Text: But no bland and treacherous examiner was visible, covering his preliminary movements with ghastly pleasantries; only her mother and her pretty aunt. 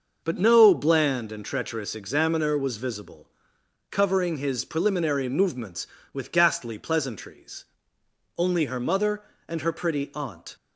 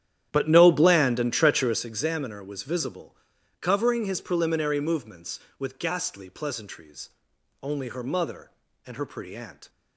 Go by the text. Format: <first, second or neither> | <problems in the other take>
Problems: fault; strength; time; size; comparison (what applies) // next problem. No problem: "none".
first | starts louder than the rest; strong; until 1.8 s; 10.5 dB